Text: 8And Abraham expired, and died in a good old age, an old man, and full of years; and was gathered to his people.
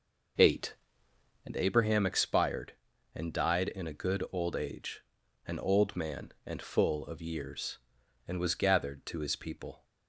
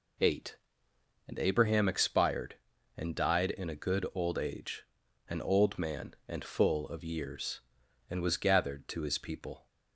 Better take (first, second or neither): second